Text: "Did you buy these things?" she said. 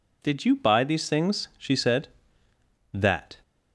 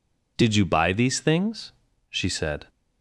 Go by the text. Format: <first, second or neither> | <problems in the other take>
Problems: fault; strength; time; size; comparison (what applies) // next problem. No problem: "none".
second | goes on to say "That"; slight; from 2.9 s on; 0.46 s long